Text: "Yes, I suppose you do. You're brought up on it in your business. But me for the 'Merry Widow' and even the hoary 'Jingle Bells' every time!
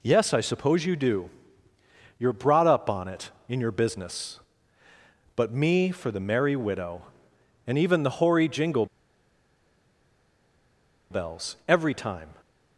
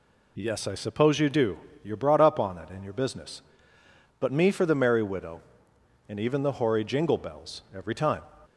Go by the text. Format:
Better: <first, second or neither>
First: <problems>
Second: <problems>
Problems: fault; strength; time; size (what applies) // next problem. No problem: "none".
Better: second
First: pauses between "Jingle" and "Bells"; strong; at 8.8 s; 2.2 s long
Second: none